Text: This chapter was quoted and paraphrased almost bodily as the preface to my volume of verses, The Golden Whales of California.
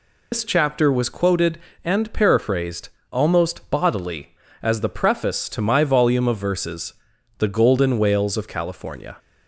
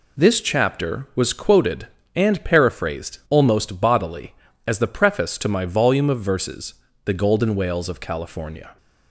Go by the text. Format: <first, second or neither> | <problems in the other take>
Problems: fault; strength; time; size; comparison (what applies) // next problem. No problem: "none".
second | loses the start of "This"; at 0.3 s; 105 ms // pauses between "paraphrased" and "almost"; slight; at 2.8 s; 0.22 s long